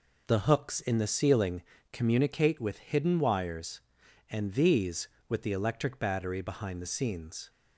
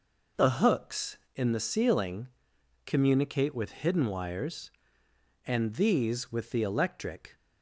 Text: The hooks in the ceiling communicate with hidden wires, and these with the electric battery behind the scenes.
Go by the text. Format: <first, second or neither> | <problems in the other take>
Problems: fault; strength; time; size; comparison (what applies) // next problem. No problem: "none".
first | pauses between "ceiling" and "communicate"; noticeable; at 2.2 s; 0.60 s long; slight in the first // stops before "battery behind the scenes"; at 7.3 s